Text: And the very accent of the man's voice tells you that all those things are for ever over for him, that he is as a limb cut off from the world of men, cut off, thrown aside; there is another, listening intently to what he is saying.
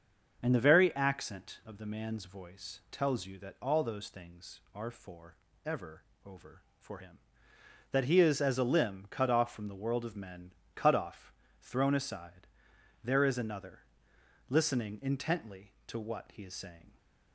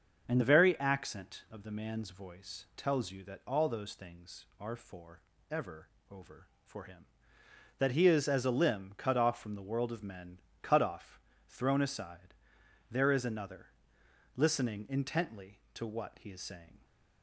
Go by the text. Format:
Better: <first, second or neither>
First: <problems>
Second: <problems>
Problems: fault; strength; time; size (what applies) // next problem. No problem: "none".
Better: neither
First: starts louder than the rest; until 1.4 s; 6.5 dB // pauses between "for" and "ever"; slight; at 5.3 s; 0.30 s long // pauses between "ever" and "over"; slight; at 6.0 s; 0.22 s long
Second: starts louder than the rest; until 1.3 s; 6.5 dB // pauses between "for" and "ever"; slight; at 5.2 s; 0.30 s long // pauses between "ever" and "over"; slight; at 5.8 s; 0.22 s long